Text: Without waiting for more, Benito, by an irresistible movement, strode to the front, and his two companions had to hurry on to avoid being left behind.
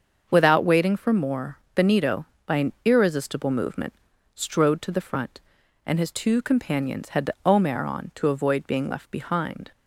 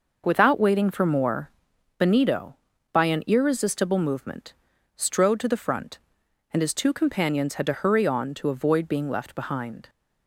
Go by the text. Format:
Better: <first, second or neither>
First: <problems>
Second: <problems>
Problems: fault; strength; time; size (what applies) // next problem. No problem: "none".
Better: second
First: starts louder than the rest; until 1.3 s; 6.5 dB // says "omer" for "hurry"; at 7.4 s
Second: none